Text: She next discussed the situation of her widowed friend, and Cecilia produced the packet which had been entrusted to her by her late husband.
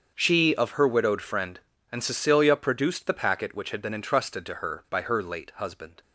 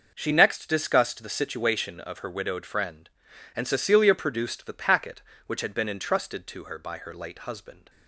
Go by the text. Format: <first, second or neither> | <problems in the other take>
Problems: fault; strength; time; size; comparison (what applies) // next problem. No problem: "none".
second | starts louder than the rest; until 1.1 s; 6.5 dB // skips "next discussed the situation"; at 0.5 s